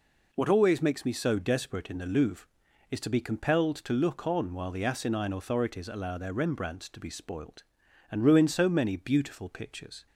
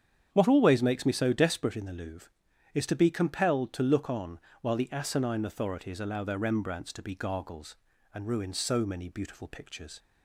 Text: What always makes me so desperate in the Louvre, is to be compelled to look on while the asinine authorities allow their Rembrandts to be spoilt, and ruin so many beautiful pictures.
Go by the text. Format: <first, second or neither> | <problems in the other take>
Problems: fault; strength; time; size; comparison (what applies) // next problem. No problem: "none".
first | starts louder than the rest; strong; until 1.3 s; 8.5 dB // pauses between "on" and "while"; slight; at 4.3 s; 0.22 s long // says "gargles" for "spoilt"; at 7.1 s